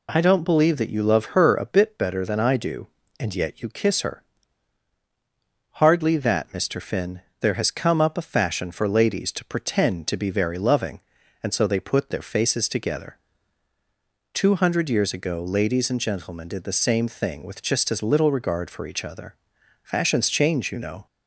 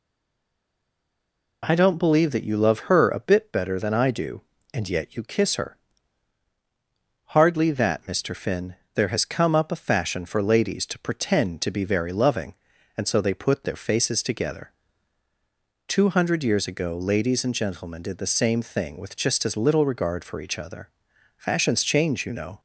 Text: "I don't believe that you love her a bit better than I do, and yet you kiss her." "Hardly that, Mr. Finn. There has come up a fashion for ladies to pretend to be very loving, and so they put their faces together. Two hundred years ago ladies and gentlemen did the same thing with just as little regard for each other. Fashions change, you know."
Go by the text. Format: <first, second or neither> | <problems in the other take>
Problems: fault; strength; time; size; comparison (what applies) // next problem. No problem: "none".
first | stays silent before the first word; noticeable; until 1.6 s; 1.6 s long